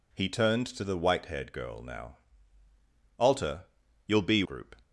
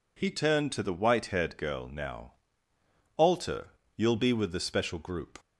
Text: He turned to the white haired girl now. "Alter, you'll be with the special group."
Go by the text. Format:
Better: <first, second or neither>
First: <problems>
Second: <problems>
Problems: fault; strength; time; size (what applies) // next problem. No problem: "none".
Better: second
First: skips "with the special"; at 4.4 s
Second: none